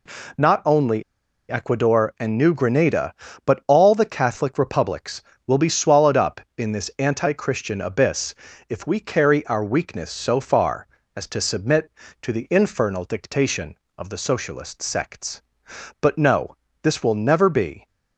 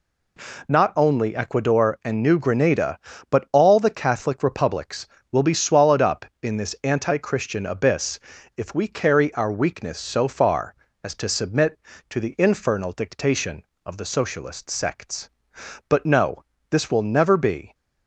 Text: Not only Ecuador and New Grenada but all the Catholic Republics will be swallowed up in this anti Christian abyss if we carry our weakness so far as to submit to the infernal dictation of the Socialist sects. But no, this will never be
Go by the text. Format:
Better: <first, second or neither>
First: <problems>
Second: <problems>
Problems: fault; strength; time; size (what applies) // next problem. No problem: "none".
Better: second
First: pauses between "only" and "Ecuador"; noticeable; at 1.0 s; 0.47 s long // pauses between "abyss" and "if"; slight; at 8.3 s; 0.34 s long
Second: pauses between "abyss" and "if"; at 8.1 s; 0.36 s long